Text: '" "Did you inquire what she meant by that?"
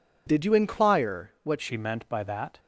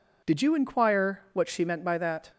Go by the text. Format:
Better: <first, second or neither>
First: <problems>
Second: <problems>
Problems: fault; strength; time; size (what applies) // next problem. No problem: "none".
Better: second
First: changes voice at "she"; from 1.6 s on; 0.9 s long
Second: none